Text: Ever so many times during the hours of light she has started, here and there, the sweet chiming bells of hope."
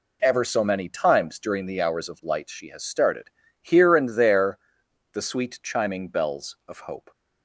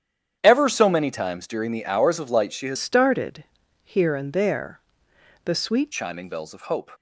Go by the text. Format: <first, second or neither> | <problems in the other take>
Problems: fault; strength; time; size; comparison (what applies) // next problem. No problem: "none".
first | starts louder than the rest; strong; until 1.4 s; 9 dB // changes voice from "started" to "sweet"; from 2.7 to 5.8 s; 3.1 s long